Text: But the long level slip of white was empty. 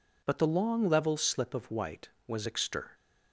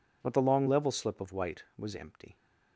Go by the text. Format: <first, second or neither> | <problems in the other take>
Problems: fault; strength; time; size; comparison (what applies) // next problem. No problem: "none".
second | says "extir" for "empty"; at 2.4 s